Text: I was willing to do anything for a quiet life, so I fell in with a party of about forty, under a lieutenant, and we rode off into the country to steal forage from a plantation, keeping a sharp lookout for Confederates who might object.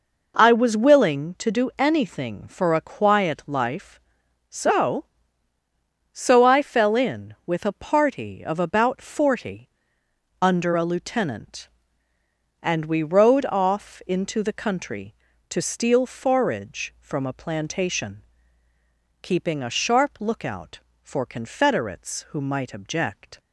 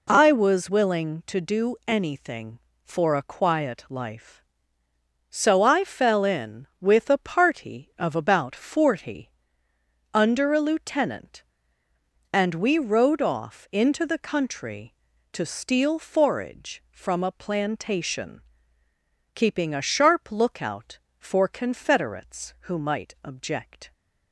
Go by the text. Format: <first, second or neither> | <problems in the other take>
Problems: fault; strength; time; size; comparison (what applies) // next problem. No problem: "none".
second | says "so" twice; at 6.1 s